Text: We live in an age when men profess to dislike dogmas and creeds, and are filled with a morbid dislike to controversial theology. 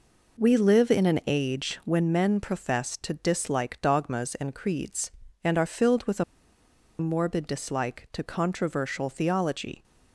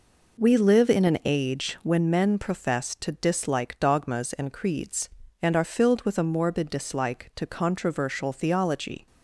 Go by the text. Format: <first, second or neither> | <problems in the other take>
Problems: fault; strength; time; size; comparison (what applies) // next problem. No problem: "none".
second | pauses between "a" and "morbid"; noticeable; at 6.2 s; 0.75 s long